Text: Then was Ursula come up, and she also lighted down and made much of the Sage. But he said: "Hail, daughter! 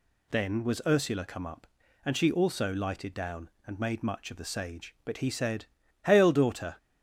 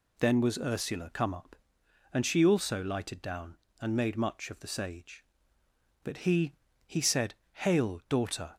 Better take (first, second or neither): first